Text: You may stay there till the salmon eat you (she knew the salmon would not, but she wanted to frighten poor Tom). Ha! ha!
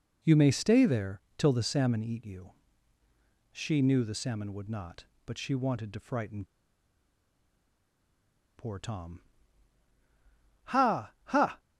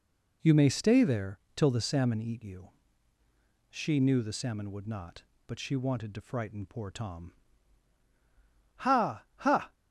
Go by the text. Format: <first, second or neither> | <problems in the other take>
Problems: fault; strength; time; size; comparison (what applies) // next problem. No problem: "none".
second | pauses between "there" and "till"; slight; at 1.1 s; 0.16 s long; slight in the second // pauses between "frighten" and "poor"; strong; at 6.4 s; 2.1 s long